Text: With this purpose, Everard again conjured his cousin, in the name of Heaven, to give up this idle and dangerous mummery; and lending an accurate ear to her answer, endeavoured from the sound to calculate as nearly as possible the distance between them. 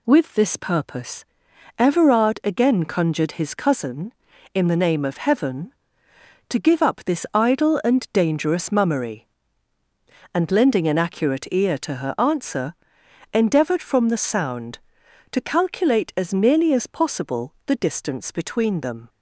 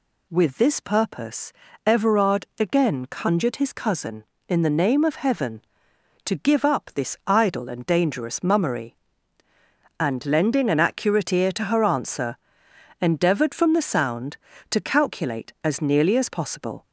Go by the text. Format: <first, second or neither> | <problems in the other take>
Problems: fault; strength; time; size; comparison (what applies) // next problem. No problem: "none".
first | stops before "the distance between them"; at 16.8 s